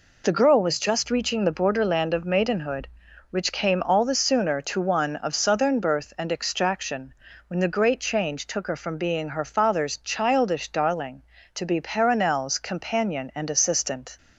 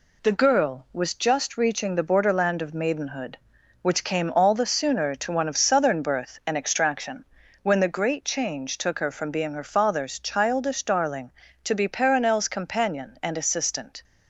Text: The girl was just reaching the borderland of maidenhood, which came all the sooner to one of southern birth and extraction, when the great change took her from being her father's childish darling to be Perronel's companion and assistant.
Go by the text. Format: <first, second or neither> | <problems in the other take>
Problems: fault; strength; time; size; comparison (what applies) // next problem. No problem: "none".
neither | none